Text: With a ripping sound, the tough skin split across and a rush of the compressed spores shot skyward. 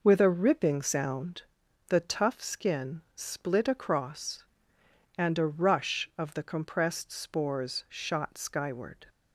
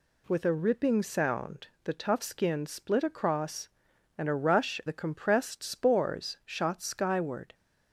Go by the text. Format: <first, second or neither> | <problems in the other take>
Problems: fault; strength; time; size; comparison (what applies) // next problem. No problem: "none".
first | skips "of"; at 4.8 s